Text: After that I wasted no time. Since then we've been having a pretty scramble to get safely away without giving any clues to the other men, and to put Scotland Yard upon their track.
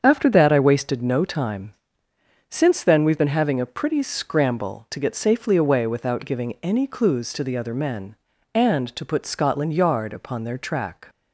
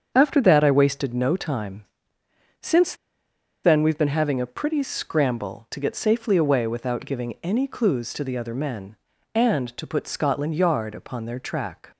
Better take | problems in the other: first | starts louder than the rest; strong; until 1.1 s; 7 dB; strong in the first // pauses between "Since" and "then"; noticeable; at 2.9 s; 0.69 s long

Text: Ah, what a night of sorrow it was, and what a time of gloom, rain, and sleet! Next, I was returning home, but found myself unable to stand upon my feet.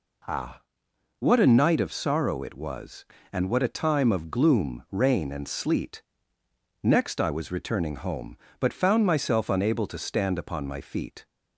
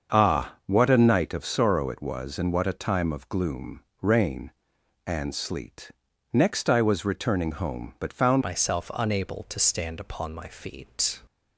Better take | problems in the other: first | starts louder than the rest; until 1.2 s; 7 dB // changes voice at "myself"; from 8.4 s on; 2.8 s long

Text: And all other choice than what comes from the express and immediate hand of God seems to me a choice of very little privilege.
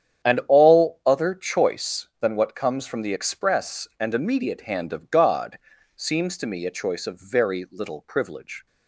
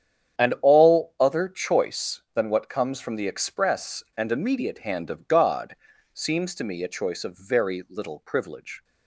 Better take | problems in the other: neither | starts louder than the rest; strong; the same in both // pauses between "God" and "seems"; the same in both

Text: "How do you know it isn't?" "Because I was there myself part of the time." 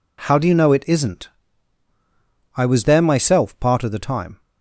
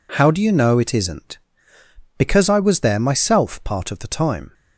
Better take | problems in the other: second | skips "Because"; at 1.9 s

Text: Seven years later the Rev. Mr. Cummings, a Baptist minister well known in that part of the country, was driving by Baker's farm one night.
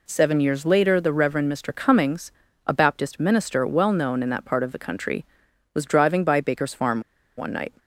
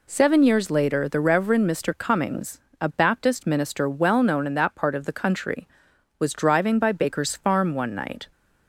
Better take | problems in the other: second | pauses between "farm" and "one"; at 7.0 s; 0.36 s long

